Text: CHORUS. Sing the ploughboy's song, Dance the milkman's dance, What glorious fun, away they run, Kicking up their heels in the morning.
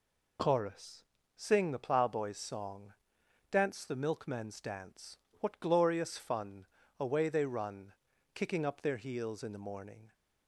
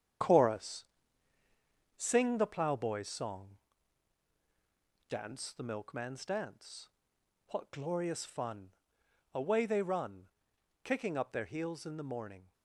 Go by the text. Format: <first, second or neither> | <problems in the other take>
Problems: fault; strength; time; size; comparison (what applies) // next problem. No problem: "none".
first | gets quieter; strong; throughout; 8.5 dB